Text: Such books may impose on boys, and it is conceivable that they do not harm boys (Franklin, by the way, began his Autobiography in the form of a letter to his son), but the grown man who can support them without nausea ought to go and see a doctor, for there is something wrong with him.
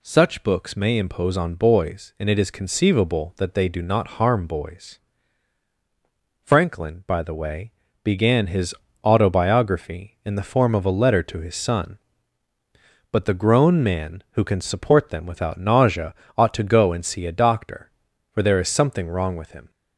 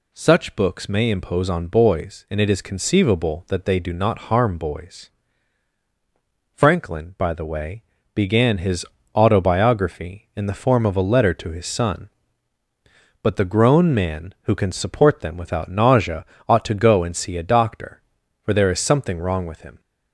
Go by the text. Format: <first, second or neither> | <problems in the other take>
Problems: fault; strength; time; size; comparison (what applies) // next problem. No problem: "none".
neither | pauses between "his" and "Autobiography"; slight; the same in both // pauses between "nausea" and "ought"; slight; the same in both